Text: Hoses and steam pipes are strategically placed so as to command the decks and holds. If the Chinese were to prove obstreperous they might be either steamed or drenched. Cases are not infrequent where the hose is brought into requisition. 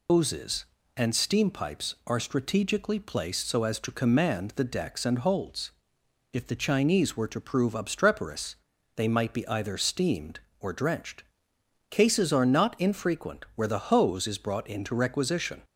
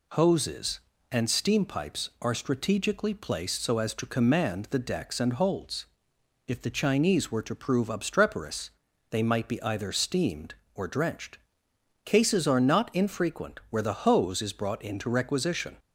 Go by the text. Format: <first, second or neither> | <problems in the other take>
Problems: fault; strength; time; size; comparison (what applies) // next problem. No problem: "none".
second | loses the start of "Hoses"; at 0.0 s; 140 ms // pauses between "obstreperous" and "they"; at 8.5 s; 0.40 s long; also in the second